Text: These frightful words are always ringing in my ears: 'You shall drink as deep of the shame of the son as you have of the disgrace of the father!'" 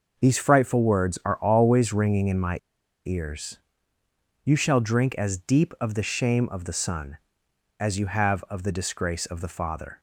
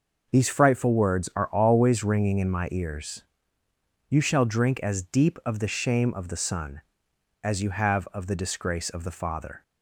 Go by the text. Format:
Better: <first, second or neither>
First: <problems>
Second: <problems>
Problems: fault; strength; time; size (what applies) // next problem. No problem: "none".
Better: second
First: pauses between "my" and "ears"; noticeable; at 2.5 s; 0.48 s long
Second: none